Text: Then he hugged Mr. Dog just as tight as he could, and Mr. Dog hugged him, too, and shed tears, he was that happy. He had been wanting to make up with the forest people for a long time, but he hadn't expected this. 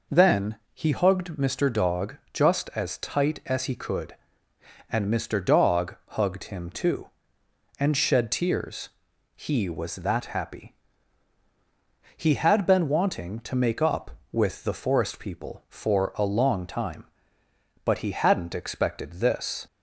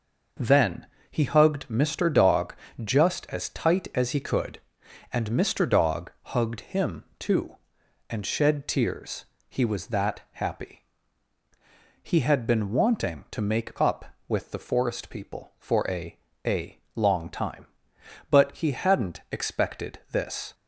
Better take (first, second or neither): first